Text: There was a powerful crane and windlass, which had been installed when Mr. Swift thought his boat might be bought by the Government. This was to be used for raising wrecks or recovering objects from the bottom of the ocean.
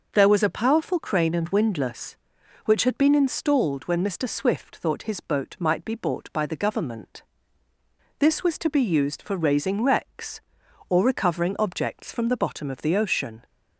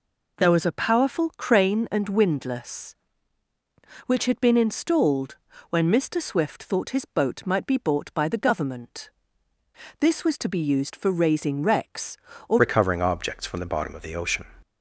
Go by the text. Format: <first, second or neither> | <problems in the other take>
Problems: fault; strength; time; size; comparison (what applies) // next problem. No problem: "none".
first | pauses between "installed" and "when"; slight; at 5.3 s; 0.34 s long // changes voice at "recovering"; from 12.5 s on; 1.9 s long